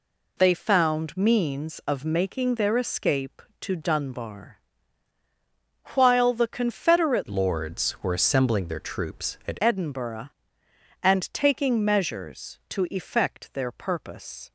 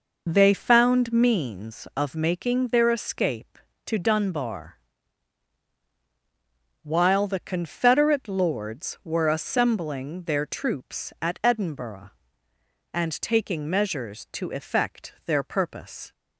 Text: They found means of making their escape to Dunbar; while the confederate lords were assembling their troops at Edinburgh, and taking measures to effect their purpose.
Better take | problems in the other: second | changes voice from "lords" to "at"; from 7.2 to 9.5 s; 2.3 s long

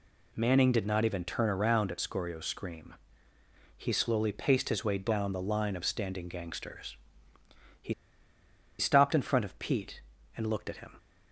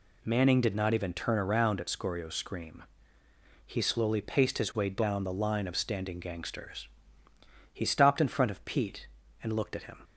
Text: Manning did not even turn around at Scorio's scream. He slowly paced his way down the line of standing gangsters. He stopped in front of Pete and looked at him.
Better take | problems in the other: second | pauses between "He" and "stopped"; noticeable; at 7.9 s; 0.85 s long

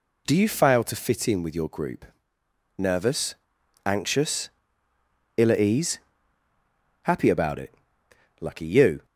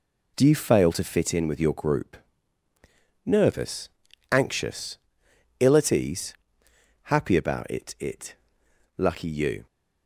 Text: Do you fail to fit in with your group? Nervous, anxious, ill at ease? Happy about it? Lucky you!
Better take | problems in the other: first | says "it" twice; at 7.9 s

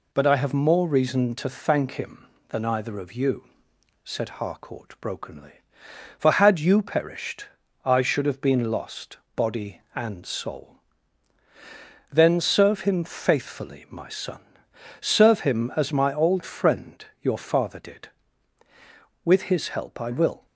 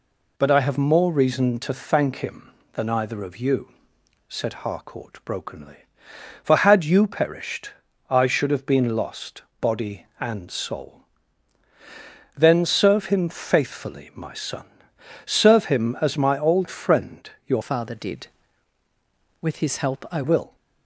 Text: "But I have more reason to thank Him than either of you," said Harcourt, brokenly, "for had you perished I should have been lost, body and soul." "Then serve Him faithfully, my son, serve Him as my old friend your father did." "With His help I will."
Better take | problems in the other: first | pauses between "perished" and "I"; at 7.6 s; 0.40 s long; also in the first // pauses between "friend" and "your"; slight; at 17.2 s; 0.16 s long; slight in the first // changes voice from "father" to "I"; from 17.6 to 20.2 s; 2.6 s long

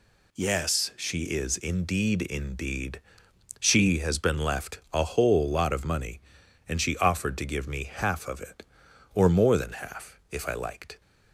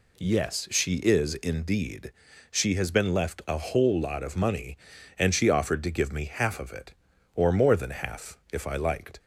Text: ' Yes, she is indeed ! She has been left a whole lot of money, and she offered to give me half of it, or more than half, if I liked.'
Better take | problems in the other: second | says "indeed" twice; at 2.2 s

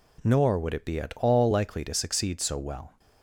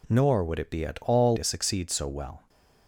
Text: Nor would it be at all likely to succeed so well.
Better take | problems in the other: first | skips "likely"; at 1.3 s

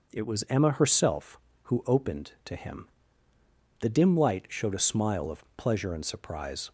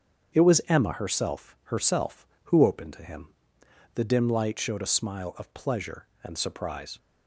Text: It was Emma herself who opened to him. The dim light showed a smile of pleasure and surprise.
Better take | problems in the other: first | starts louder than the rest; strong; until 1.4 s; 7 dB // says "herself" twice; at 1.6 s

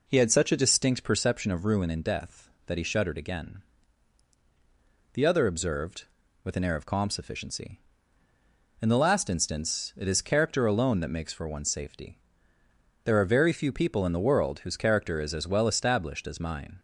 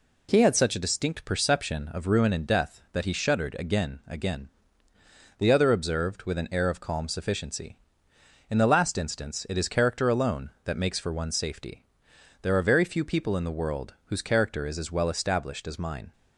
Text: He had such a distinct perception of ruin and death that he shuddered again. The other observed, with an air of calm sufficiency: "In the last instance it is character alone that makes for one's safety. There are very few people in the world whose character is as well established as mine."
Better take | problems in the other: first | says "again" twice; at 4.0 s

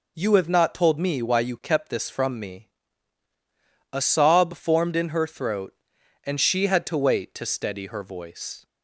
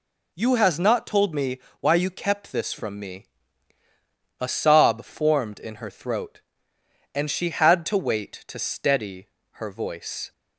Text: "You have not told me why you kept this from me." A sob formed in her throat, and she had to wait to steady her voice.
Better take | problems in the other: first | says "has" for "have"; at 0.5 s // pauses between "me" and "why"; slight; at 1.5 s; 0.22 s long // pauses between "steady" and "her"; slight; at 9.2 s; 0.28 s long

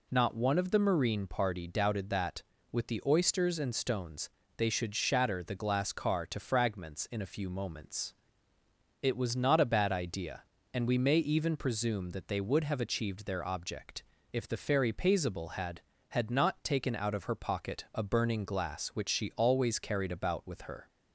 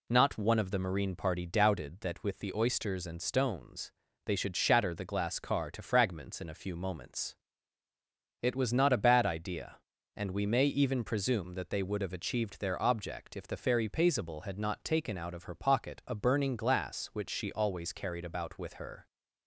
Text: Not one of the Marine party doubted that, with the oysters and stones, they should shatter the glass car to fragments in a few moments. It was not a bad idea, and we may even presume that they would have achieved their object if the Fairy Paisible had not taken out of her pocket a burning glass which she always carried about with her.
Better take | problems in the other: second | pauses between "object" and "if"; slight; at 14.0 s; 0.28 s long // says "had" twice; at 16.0 s

